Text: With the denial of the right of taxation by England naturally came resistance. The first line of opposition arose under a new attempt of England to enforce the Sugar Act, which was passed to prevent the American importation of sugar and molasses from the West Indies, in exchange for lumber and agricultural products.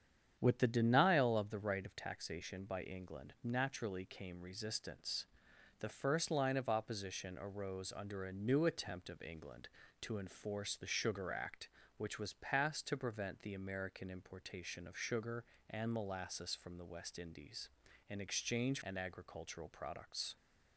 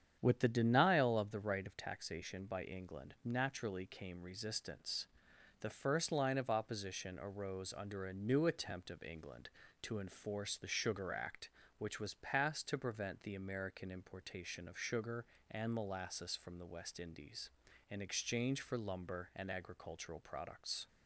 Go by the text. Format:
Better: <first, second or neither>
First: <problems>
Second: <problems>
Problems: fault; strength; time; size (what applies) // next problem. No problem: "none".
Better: second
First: starts louder than the rest; strong; until 1.4 s; 8.5 dB // skips "for lumber"; at 18.8 s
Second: starts louder than the rest; strong; until 1.2 s; 8.5 dB